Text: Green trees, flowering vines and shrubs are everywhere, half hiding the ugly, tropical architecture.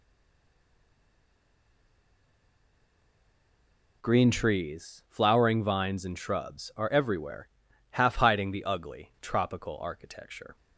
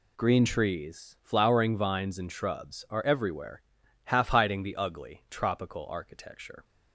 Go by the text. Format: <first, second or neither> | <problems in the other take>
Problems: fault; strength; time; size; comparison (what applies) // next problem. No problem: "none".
second | stays silent before the first word; strong; until 4.0 s; 4.0 s long